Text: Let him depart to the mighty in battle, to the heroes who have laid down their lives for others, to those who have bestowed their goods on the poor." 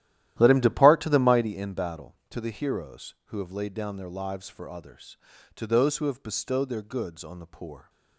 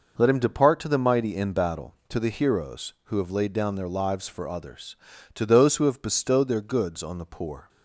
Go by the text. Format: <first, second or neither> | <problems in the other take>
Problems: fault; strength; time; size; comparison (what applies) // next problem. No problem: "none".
second | starts louder than the rest; strong; until 1.6 s; 13 dB